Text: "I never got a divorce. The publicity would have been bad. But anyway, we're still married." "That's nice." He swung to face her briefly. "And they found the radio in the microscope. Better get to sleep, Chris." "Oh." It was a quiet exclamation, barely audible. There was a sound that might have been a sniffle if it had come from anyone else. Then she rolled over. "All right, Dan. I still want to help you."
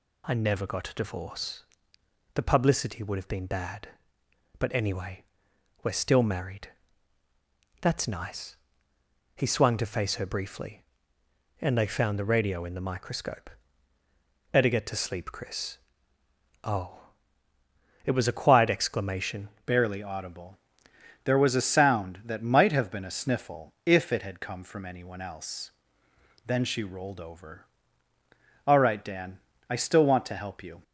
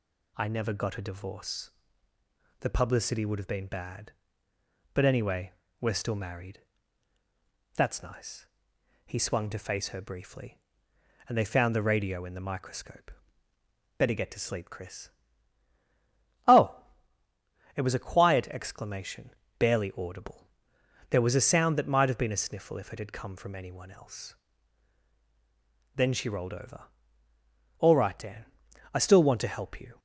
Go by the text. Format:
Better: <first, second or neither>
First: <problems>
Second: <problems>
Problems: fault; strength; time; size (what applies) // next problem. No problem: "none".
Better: second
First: changes voice at "barely"; from 19.6 s on; 11.2 s long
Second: none